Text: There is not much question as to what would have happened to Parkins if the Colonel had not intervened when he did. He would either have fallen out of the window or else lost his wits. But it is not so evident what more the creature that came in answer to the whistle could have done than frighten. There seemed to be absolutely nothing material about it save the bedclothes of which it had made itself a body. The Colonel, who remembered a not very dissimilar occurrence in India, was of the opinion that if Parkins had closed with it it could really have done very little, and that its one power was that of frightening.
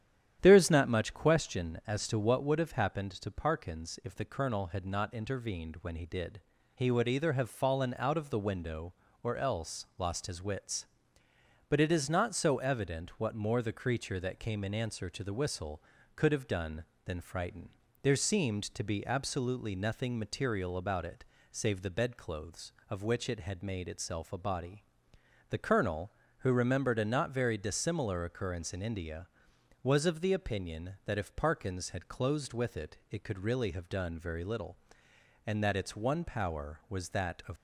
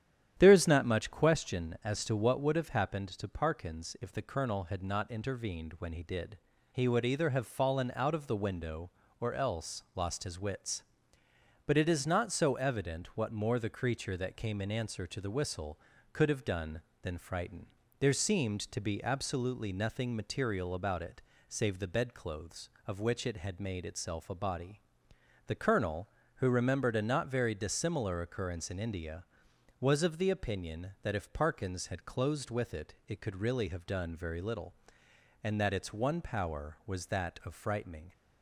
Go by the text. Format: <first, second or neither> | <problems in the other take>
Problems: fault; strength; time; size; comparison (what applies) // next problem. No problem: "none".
second | starts louder than the rest; strong; until 1.4 s; 10.5 dB; strong in the second // pauses between "it" and "save"; slight; at 21.2 s; 0.28 s long; slight in the second // stops before "frightening"; at 37.5 s